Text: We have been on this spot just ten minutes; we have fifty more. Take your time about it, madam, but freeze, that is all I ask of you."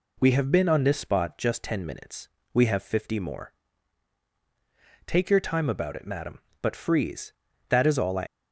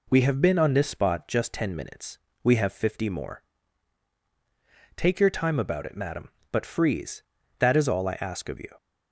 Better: second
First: stops before "ask of you"; at 8.2 s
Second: none

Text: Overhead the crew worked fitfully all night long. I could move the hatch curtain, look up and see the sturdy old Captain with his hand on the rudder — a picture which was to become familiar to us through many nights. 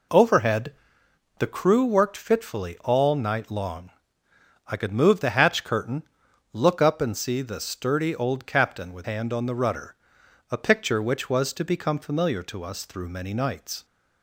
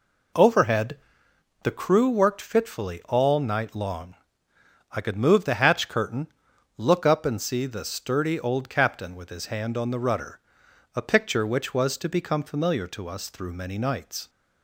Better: second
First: pauses between "Overhead" and "the"; noticeable; at 0.7 s; 0.62 s long // skips "his"; at 9.0 s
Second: pauses between "Overhead" and "the"; noticeable; at 0.9 s; 0.62 s long

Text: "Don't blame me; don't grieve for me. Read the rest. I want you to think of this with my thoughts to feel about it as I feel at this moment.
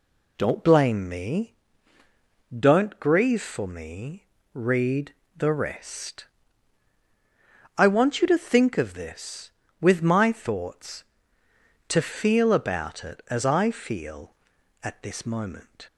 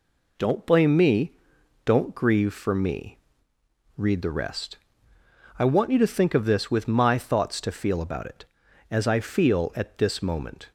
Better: second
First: changes voice at "blame"; from 0.6 s on; 15.2 s long // pauses between "Read" and "the"; slight; at 5.1 s; 0.20 s long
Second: none

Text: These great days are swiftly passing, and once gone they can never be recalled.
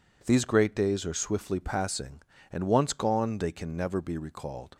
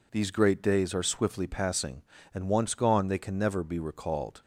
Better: neither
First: none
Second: none

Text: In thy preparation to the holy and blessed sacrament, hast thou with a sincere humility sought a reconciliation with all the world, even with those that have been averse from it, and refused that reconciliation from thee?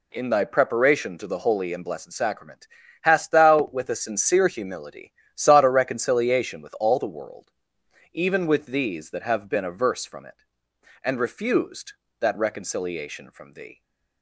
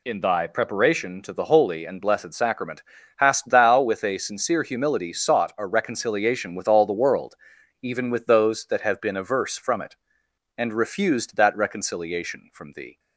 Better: second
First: pauses between "humility" and "sought"; slight; at 5.1 s; 0.22 s long // says "these" for "those"; at 8.6 s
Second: none

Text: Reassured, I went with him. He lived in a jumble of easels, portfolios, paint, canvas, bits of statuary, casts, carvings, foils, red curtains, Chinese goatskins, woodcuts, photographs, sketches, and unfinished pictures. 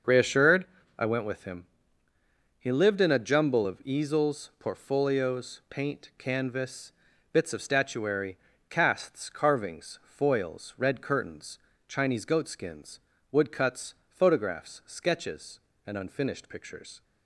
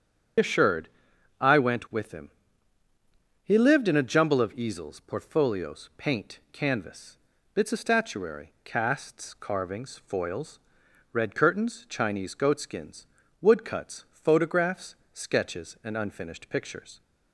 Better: first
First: starts louder than the rest; noticeable; until 1.4 s; 6 dB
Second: loses the start of "Reassured"; at 0.3 s; 155 ms // starts louder than the rest; strong; until 1.9 s; 8 dB

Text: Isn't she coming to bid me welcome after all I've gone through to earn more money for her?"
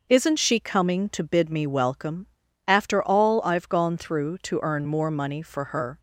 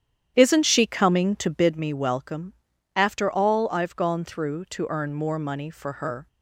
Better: first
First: pauses between "welcome" and "after"; at 2.2 s; 0.40 s long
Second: starts louder than the rest; strong; until 1.8 s; 10 dB // pauses between "welcome" and "after"; at 2.5 s; 0.42 s long

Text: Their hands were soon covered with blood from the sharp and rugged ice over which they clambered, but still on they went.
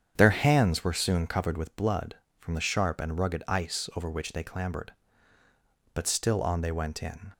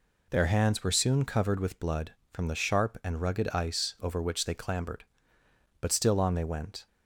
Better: second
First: starts louder than the rest; strong; until 1.1 s; 8 dB // goes on to say "In"; slight; from 7.0 s on; 0.30 s long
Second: none

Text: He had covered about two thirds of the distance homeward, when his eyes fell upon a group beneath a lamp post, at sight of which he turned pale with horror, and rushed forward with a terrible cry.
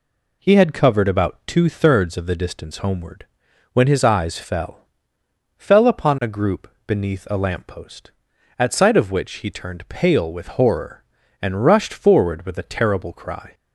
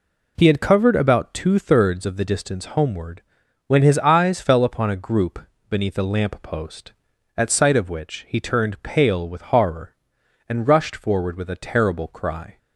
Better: second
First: says "fell" twice; at 5.5 s // pauses between "group" and "beneath"; slight; at 6.6 s; 0.22 s long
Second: pauses between "group" and "beneath"; slight; at 5.3 s; 0.30 s long

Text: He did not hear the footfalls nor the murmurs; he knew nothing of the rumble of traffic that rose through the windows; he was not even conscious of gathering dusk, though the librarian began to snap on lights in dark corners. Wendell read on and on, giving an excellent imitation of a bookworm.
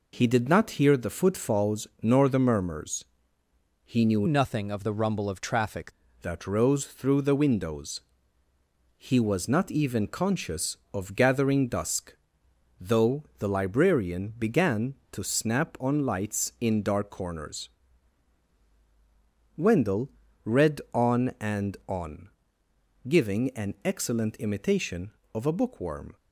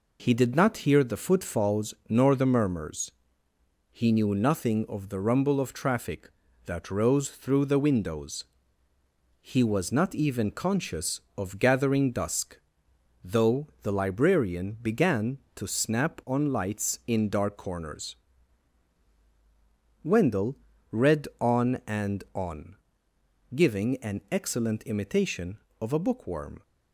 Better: second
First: changes voice from "nothing" to "traffic"; from 4.2 to 5.9 s; 1.7 s long // pauses between "Wendell" and "read"; slight; at 20.0 s; 0.34 s long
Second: pauses between "Wendell" and "read"; slight; at 20.5 s; 0.34 s long

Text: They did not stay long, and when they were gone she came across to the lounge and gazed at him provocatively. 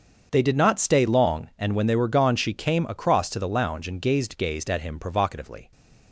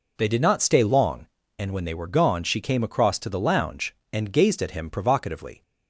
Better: second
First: starts louder than the rest; until 1.3 s; 7 dB // says "gazed" twice; at 4.3 s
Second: none

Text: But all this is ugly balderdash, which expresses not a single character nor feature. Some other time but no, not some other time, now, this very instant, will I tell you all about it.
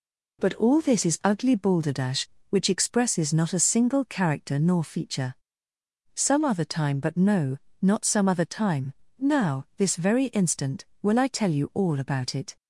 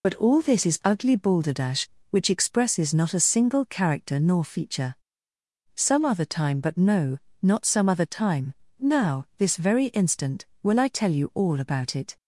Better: first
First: none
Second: loses the start of "But"; at 0.0 s; 55 ms

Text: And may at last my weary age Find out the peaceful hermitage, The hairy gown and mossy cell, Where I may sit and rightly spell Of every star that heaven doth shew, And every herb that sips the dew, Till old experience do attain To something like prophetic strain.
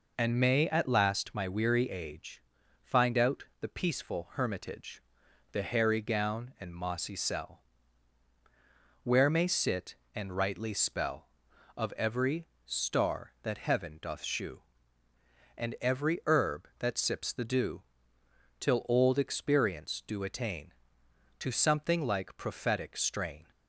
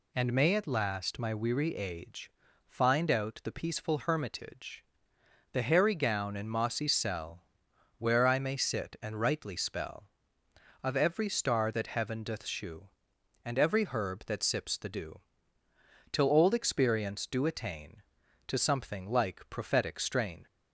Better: second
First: pauses between "age" and "Find"; at 2.4 s; 0.40 s long // pauses between "out" and "the"; slight; at 3.4 s; 0.18 s long // skips "I"; at 9.2 s // pauses between "every" and "star"; slight; at 12.4 s; 0.20 s long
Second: pauses between "age" and "Find"; at 2.2 s; 0.38 s long

